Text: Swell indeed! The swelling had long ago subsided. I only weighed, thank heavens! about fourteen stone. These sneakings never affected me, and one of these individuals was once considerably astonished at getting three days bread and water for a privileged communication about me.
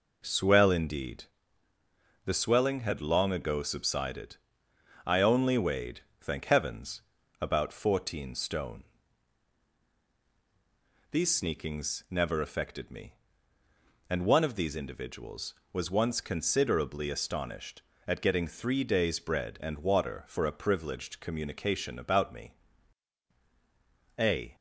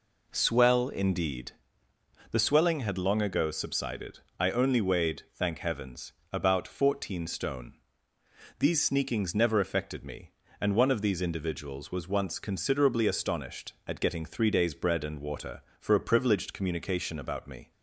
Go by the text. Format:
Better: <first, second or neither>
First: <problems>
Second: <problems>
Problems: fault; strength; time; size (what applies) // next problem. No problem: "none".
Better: second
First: goes on to say "A"; slight; from 24.1 s on; 0.38 s long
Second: none